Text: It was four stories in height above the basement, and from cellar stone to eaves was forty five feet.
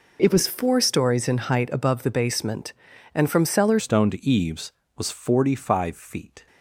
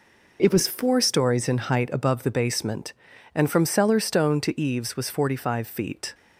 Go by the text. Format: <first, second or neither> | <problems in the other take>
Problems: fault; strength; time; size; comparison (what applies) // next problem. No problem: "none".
second | changes voice at "stone"; from 3.7 s on; 2.7 s long